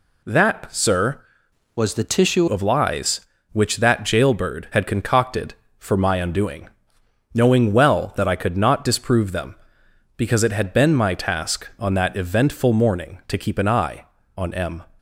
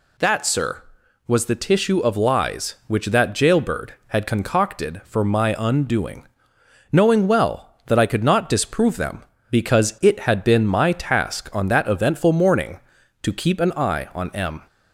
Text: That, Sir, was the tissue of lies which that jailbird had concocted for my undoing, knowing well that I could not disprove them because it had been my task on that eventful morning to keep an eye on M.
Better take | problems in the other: second | changes voice from "was" to "tissue"; from 1.7 to 2.4 s; 0.7 s long

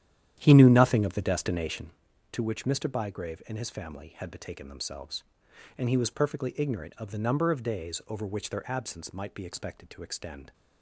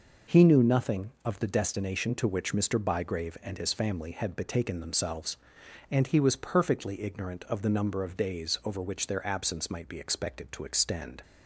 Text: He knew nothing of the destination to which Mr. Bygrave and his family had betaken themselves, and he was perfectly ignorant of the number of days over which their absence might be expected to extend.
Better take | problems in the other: second | starts louder than the rest; strong; until 2.0 s; 10.5 dB

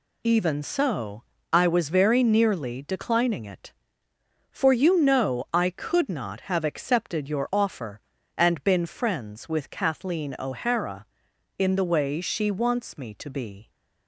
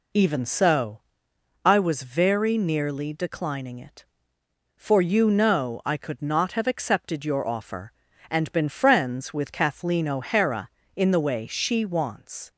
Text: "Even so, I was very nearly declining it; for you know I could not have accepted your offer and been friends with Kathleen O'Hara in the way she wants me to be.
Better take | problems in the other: first | stops before "me to be"; at 12.4 s

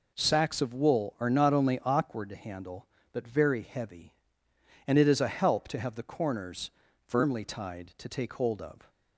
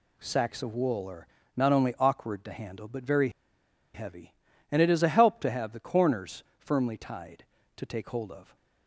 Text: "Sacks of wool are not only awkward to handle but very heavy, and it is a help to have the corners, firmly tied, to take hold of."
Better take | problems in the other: first | pauses between "are" and "not"; slight; at 1.2 s; 0.28 s long // pauses between "very" and "heavy"; noticeable; at 3.2 s; 0.65 s long

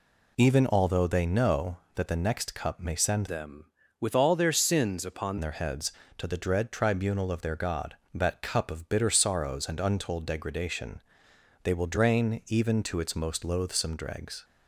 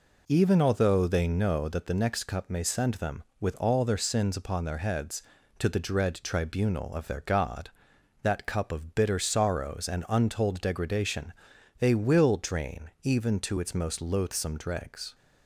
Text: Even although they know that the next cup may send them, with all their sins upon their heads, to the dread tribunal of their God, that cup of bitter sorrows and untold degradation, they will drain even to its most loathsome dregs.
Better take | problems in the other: second | changes voice from "them" to "upon"; from 3.2 to 5.3 s; 2.1 s long

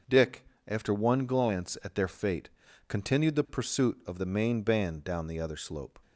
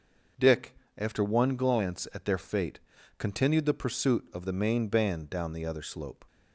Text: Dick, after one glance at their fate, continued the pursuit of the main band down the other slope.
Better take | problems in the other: neither | none

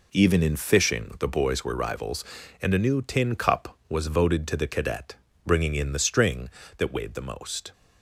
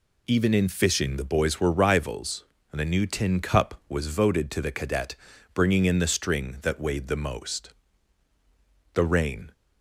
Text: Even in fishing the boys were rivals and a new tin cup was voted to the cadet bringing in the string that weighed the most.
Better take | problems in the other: first | pauses between "cadet" and "bringing"; at 5.1 s; 0.38 s long; slight in the first // goes on to say "The rain"; from 8.9 s on; 0.58 s long

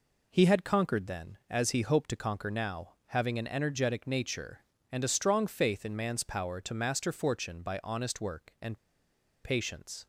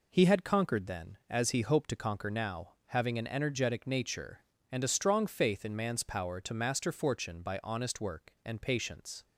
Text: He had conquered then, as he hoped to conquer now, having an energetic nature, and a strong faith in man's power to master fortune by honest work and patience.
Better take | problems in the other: second | pauses between "and" and "patience"; noticeable; at 8.7 s; 0.66 s long

